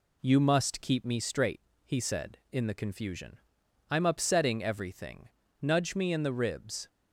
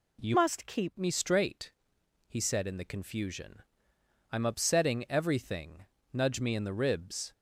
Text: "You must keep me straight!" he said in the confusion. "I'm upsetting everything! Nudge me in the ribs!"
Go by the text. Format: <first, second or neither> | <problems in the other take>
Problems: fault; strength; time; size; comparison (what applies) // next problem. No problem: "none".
first | changes voice from "must" to "keep"; from 0.3 to 0.9 s; 0.6 s long